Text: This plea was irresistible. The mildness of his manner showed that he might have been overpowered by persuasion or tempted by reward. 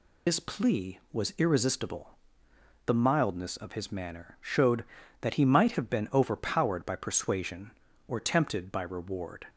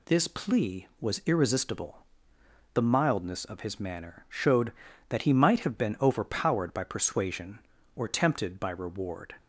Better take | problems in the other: second | loses the start of "This"; at 0.2 s; 80 ms

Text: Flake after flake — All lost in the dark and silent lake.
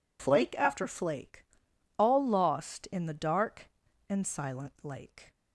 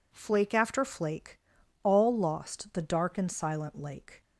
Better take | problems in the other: first | skips "in"; at 2.7 s

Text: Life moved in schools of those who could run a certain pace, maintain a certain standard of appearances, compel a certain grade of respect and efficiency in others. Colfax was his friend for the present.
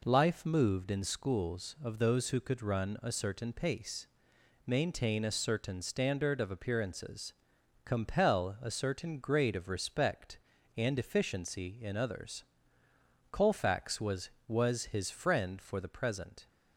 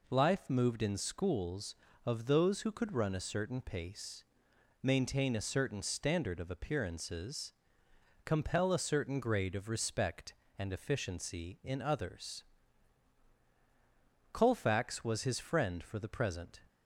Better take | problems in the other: second | says "was" twice; at 14.4 s

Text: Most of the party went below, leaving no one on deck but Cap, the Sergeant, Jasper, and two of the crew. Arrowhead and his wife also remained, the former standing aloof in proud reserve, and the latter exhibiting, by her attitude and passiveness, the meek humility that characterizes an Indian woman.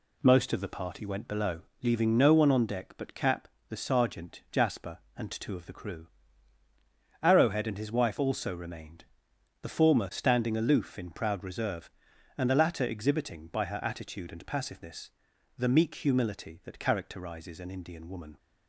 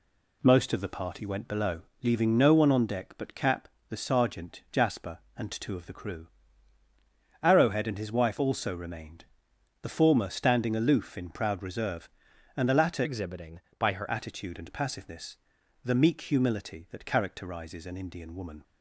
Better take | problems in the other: first | changes voice from "exhibiting" to "her"; from 13.0 to 14.0 s; 1.0 s long

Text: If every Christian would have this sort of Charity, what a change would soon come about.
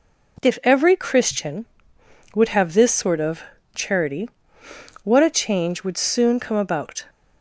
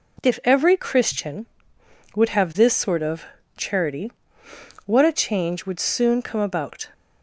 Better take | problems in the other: neither | pauses between "of" and "Charity"; slight; the same in both

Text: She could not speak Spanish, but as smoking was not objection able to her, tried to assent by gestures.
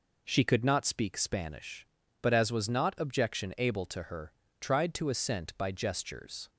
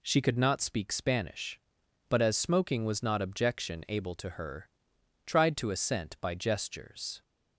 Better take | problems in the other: second | skips "smoking"; at 2.5 s

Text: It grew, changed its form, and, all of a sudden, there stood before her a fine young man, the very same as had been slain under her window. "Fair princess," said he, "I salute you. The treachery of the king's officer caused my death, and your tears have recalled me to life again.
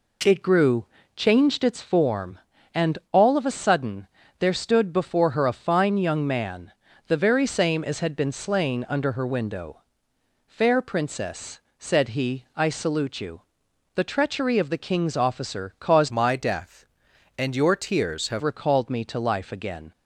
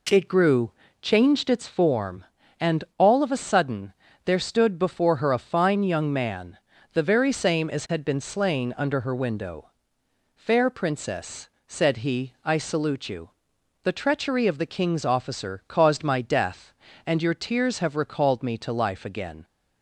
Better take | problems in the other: second | changes voice from "my" to "have"; from 16.0 to 18.4 s; 2.4 s long

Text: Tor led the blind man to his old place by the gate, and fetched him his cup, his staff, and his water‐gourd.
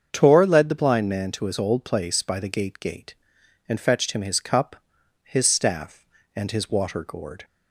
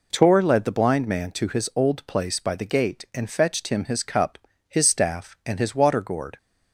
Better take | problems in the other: second | starts louder than the rest; until 1.1 s; 7 dB // says "gate" twice; at 2.8 s

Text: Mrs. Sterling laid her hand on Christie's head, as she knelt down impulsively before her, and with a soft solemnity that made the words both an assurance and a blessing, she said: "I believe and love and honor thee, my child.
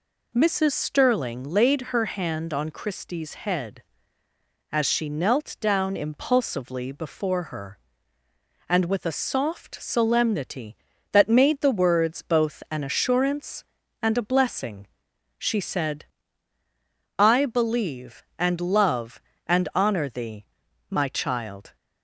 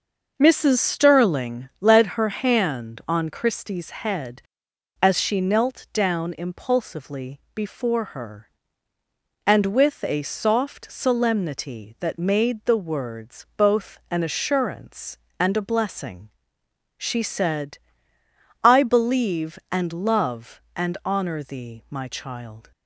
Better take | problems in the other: first | starts louder than the rest; noticeable; until 1.3 s; 6 dB // says "led" for "laid"; at 1.7 s

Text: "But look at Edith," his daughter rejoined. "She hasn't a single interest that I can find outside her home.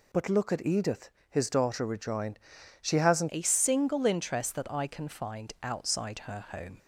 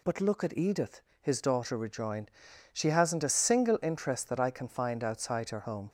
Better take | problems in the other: second | changes voice at "a"; from 3.2 s on; 3.5 s long

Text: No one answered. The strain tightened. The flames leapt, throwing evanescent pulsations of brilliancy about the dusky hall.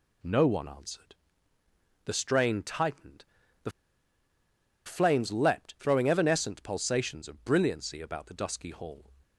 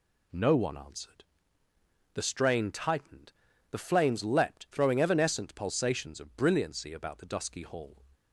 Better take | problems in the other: second | pauses between "The" and "flames"; at 3.7 s; 1.1 s long

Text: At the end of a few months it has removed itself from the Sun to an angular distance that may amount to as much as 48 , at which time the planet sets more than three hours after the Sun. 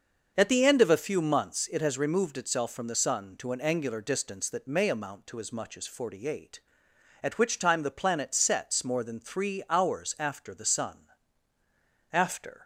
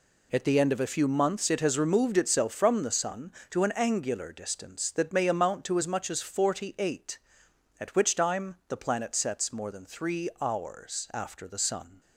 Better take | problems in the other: second | starts louder than the rest; until 1.3 s; 6 dB // goes on to say "After"; from 12.1 s on; 0.50 s long

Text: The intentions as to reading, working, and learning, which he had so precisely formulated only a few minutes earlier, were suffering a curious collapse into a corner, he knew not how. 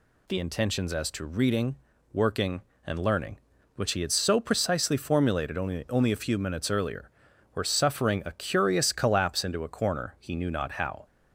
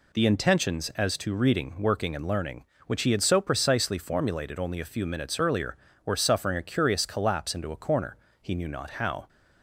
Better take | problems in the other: second | says "only" twice; at 5.8 s

